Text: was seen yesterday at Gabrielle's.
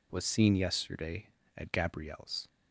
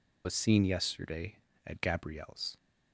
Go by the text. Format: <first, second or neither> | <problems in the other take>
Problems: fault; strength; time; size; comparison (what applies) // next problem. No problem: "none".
first | loses the start of "was"; at 0.2 s; 60 ms